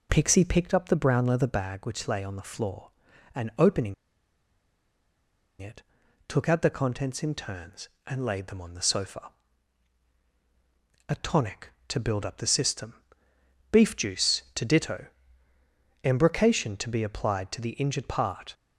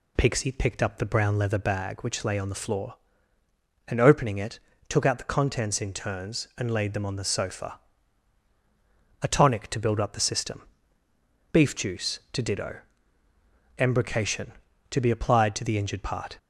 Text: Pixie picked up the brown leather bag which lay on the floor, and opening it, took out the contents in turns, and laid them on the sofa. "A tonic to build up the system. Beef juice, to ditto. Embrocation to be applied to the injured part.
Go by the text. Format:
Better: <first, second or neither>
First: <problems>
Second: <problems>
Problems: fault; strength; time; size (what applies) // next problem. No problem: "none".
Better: second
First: pauses between "opening" and "it"; strong; at 3.9 s; 1.6 s long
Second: none